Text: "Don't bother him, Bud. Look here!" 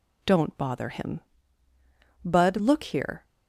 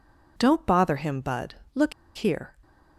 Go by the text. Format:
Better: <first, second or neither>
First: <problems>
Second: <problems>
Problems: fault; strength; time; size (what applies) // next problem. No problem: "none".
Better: first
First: none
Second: pauses between "Look" and "here"; slight; at 1.9 s; 0.24 s long